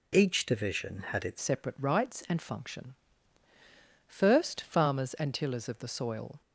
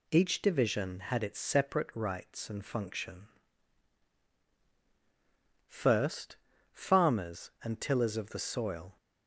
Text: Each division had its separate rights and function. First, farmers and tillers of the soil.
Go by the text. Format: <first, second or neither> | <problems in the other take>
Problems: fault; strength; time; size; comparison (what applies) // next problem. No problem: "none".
second | changes voice at "separate"; from 1.3 s on; 5.1 s long